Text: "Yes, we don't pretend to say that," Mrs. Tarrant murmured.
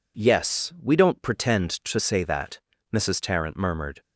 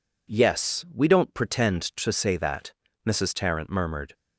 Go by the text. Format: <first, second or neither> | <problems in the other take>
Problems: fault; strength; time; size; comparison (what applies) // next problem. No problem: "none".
neither | none